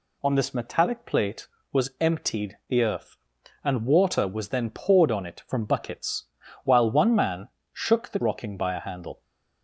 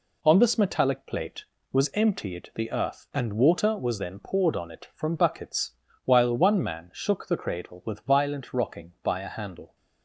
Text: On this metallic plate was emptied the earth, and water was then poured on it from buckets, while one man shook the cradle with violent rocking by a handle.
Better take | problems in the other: second | pauses between "man" and "shook"; slight; at 7.4 s; 0.26 s long // skips "cradle with violent"; at 8.2 s

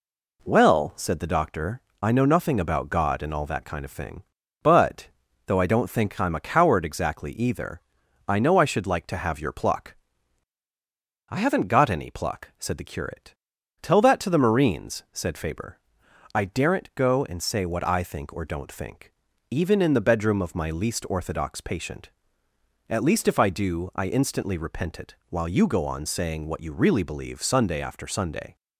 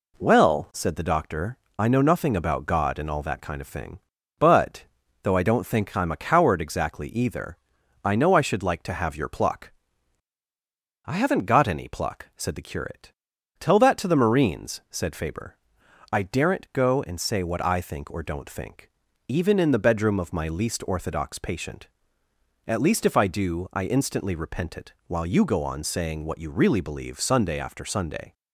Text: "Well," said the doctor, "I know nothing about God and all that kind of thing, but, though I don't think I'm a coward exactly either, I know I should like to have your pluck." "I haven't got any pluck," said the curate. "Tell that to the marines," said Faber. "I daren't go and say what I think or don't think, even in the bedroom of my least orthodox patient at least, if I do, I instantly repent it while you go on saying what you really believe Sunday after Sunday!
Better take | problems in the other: neither | pauses between "it" and "while"; slight; the same in both

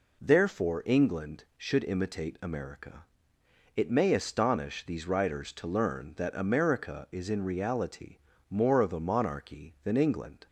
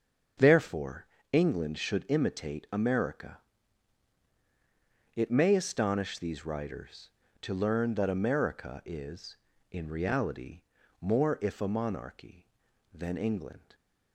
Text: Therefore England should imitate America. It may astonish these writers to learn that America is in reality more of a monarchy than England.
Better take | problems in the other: first | starts louder than the rest; strong; until 1.6 s; 7 dB // pauses between "Therefore" and "England"; slight; at 1.0 s; 0.28 s long // pauses between "reality" and "more"; at 10.6 s; 0.40 s long; slight in the first // says "if" for "of"; at 11.4 s

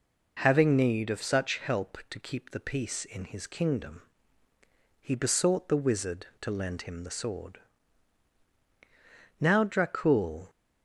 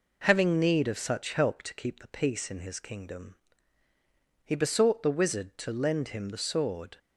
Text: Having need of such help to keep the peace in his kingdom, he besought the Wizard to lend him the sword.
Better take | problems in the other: second | goes on to say "Now Dracul"; noticeable; from 9.3 s on; 1.1 s long

